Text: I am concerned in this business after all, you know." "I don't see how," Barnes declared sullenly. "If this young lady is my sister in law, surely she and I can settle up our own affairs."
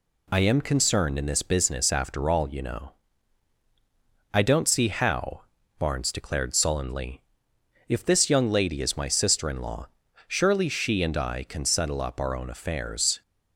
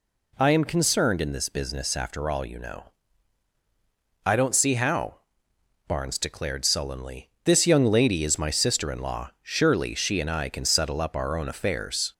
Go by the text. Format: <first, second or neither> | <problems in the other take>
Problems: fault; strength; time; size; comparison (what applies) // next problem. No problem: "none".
first | skips "If"; at 7.3 s